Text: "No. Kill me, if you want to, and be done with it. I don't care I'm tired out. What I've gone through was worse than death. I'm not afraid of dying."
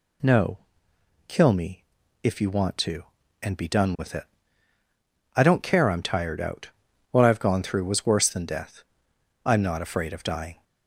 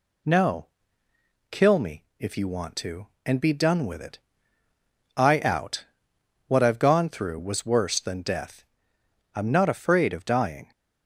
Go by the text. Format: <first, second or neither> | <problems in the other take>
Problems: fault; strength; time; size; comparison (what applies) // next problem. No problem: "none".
first | skips "don't care I'm tired"; at 5.3 s